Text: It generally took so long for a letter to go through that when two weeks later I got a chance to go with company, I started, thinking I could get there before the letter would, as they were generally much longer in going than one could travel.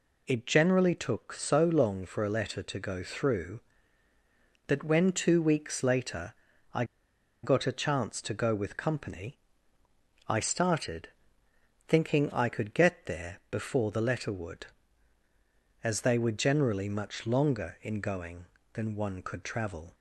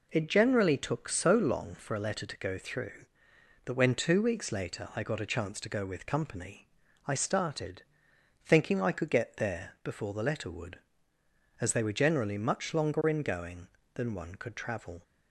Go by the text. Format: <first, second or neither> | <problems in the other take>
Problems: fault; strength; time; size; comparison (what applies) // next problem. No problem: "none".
second | pauses between "later" and "I"; at 6.3 s; 0.38 s long // pauses between "I" and "got"; noticeable; at 6.8 s; 0.59 s long